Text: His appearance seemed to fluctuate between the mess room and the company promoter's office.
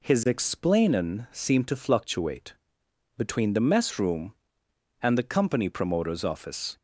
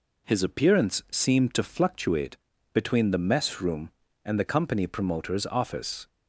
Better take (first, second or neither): second